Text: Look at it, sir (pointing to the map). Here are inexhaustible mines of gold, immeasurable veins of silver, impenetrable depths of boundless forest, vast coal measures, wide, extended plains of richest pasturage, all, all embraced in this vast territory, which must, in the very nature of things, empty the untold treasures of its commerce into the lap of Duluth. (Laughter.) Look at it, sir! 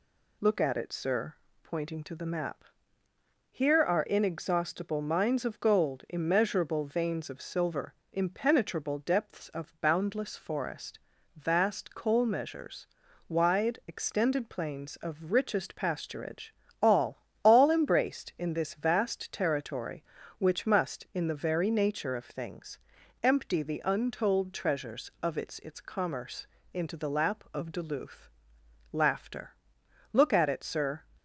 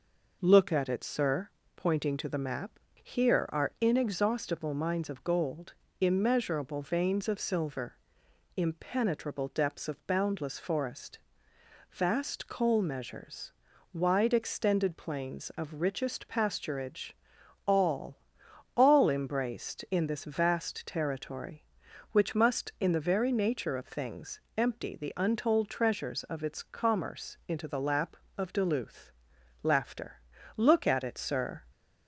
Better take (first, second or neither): second